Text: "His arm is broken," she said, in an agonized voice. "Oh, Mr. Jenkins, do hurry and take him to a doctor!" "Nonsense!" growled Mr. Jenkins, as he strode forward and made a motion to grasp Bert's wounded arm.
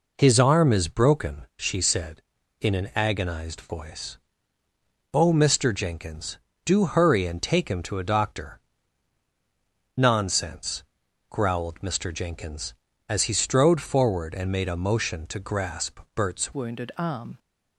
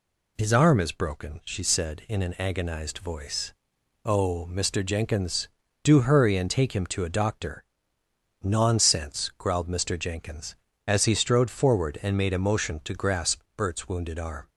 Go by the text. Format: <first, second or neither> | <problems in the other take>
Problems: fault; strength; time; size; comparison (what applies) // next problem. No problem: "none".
second | changes voice at "wounded"; from 16.5 s on; 0.8 s long